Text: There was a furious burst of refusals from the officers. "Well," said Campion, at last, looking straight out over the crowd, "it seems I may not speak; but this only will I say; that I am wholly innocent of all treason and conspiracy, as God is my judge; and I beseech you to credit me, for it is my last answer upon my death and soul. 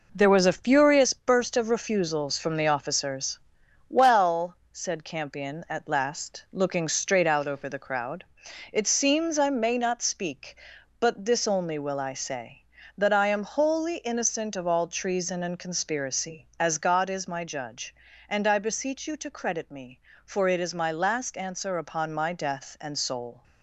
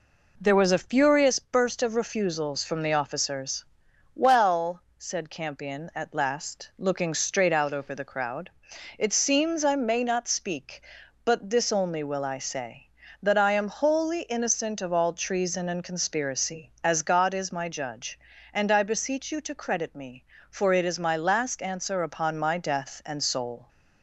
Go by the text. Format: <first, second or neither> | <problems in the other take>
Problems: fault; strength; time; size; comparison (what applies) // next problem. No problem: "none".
second | gets quieter; noticeable; throughout; 5 dB